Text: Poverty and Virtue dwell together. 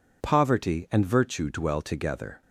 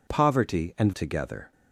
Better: first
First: none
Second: skips "Virtue dwell"; at 0.9 s

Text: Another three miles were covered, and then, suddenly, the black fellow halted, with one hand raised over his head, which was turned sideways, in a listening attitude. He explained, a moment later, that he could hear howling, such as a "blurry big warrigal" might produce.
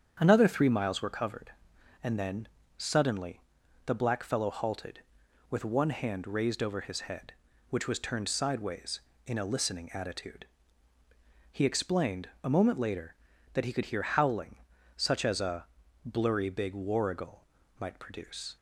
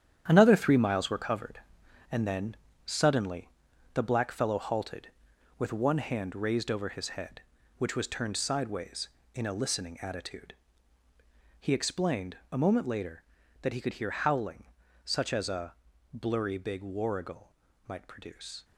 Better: first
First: starts louder than the rest; strong; until 1.2 s; 8 dB // pauses between "a" and "blurry"; at 15.6 s; 0.38 s long // pauses between "warrigal" and "might"; slight; at 17.4 s; 0.34 s long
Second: gets quieter; strong; throughout; 9 dB // starts louder than the rest; strong; until 1.2 s; 9.5 dB // pauses between "a" and "blurry"; at 15.7 s; 0.38 s long // pauses between "warrigal" and "might"; slight; at 17.5 s; 0.34 s long

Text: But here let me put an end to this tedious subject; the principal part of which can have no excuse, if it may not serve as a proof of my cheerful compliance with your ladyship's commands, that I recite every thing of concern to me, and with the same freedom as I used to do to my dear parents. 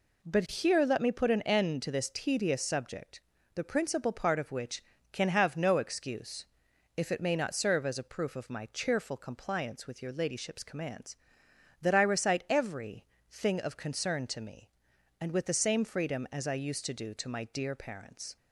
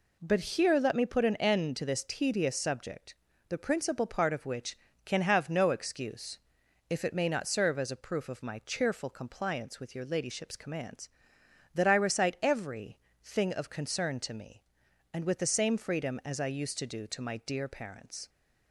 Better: neither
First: pauses between "every" and "thing"; slight; at 13.0 s; 0.26 s long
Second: pauses between "every" and "thing"; slight; at 12.9 s; 0.26 s long

